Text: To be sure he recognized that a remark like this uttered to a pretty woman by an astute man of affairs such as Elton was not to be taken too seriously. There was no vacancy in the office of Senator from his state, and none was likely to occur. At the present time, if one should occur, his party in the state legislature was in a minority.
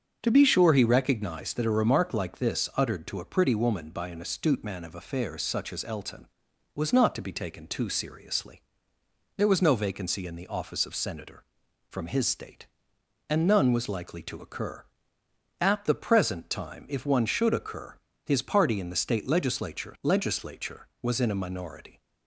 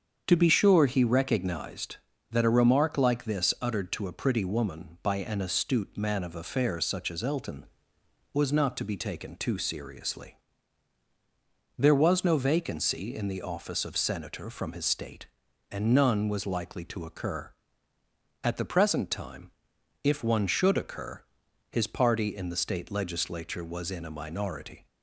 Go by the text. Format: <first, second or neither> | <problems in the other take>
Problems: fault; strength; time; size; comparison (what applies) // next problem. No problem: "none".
second | starts louder than the rest; until 1.2 s; 7 dB; strong in the second // says "legislature" twice; at 20.0 s